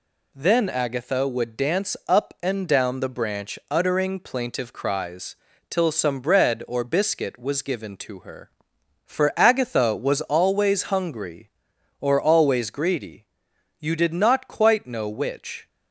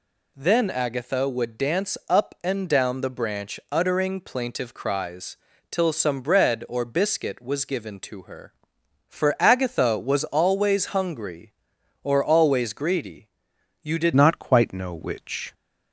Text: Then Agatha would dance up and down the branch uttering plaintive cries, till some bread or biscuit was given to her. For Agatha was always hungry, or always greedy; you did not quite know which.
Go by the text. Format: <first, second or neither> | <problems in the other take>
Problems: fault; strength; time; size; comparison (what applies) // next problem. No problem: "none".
first | changes voice at "not"; from 14.1 s on; 1.4 s long